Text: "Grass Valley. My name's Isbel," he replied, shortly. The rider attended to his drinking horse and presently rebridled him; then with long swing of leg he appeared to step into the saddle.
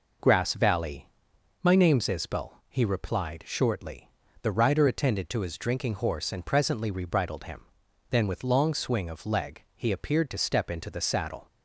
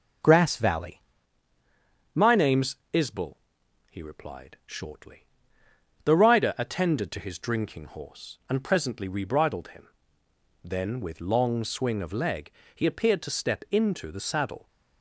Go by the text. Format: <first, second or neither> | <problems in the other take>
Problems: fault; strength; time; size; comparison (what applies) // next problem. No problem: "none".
first | changes voice at "My"; from 2.1 s on; 12.5 s long // pauses between "name's" and "Isbel"; slight; at 2.7 s; 0.16 s long // pauses between "leg" and "he"; slight; at 12.5 s; 0.24 s long